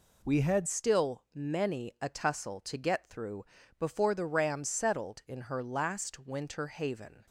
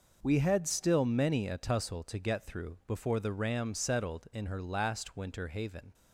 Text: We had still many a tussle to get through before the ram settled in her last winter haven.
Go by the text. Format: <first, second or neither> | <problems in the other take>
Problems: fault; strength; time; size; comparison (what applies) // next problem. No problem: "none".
second | changes voice at "still"; from 0.6 s on; 6.6 s long // pauses between "through" and "before"; slight; at 3.4 s; 0.34 s long